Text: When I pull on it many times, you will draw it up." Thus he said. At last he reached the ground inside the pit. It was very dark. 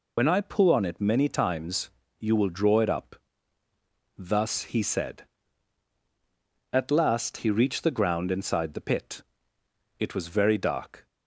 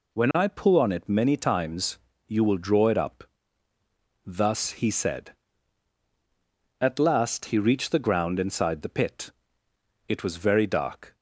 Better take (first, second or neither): second